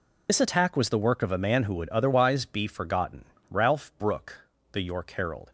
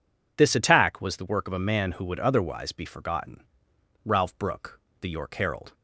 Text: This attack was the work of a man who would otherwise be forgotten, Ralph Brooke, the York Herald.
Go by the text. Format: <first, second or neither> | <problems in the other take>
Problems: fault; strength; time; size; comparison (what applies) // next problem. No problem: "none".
second | loses the start of "This"; at 0.2 s; 70 ms